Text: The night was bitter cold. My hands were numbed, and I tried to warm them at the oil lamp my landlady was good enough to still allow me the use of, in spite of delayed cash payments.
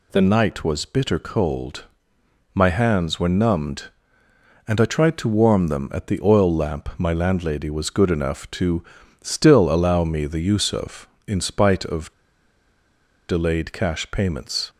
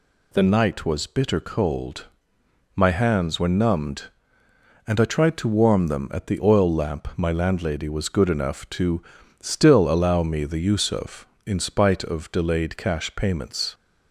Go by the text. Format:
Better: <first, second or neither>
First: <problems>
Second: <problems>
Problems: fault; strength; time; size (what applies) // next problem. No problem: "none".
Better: second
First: pauses between "to" and "still"; at 8.8 s; 0.38 s long // pauses between "of" and "delayed"; at 12.1 s; 1.1 s long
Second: pauses between "to" and "still"; at 9.0 s; 0.38 s long